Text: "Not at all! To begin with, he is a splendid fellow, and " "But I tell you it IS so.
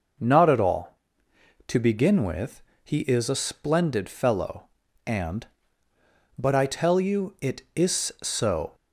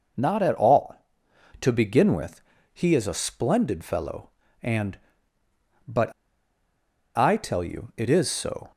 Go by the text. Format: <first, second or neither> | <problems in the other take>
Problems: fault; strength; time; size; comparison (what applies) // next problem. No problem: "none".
first | starts louder than the rest; noticeable; until 1.8 s; 6 dB; noticeable in the first // pauses between "But" and "I"; at 6.1 s; 1.0 s long